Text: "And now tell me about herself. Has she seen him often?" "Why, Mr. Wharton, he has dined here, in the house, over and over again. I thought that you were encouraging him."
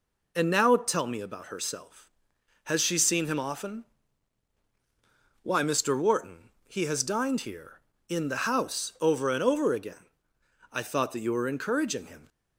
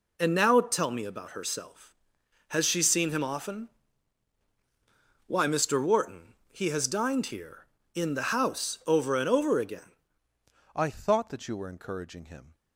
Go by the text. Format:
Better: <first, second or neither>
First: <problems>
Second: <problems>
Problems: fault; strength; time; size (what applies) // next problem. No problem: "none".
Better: first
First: none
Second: changes voice at "I"; from 10.7 s on; 1.8 s long